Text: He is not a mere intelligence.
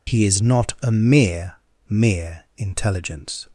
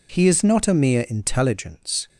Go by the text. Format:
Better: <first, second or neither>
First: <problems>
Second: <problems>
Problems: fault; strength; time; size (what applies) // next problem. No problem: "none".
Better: second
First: says "mere" twice; at 1.8 s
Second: none